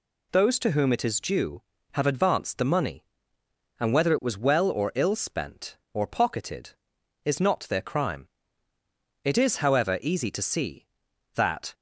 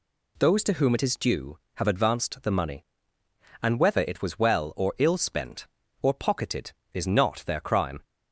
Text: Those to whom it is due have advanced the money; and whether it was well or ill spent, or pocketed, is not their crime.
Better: second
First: goes on to say "It is however easy to see that"; strong; from 9.2 s on; 2.4 s long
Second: none

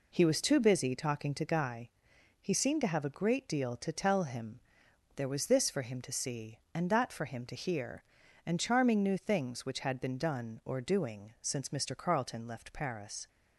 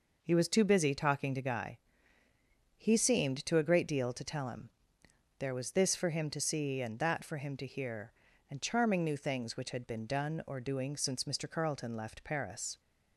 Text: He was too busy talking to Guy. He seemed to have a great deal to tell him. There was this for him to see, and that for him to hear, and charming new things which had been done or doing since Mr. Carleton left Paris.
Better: first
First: none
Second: skips "have"; at 3.5 s

